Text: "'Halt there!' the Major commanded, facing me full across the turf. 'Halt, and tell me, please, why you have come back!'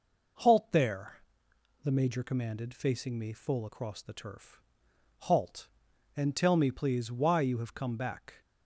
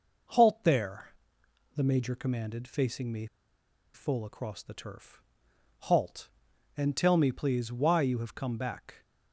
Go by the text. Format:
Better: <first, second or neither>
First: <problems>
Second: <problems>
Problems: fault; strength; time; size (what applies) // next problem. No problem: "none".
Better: first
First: none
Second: pauses between "me" and "full"; noticeable; at 3.2 s; 0.68 s long